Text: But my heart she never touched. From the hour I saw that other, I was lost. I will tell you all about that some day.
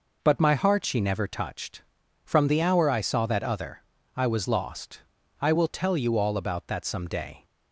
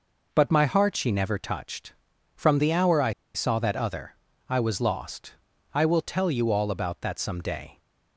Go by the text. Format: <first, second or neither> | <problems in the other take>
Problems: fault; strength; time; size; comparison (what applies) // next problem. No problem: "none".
first | pauses between "I" and "saw"; slight; at 3.1 s; 0.24 s long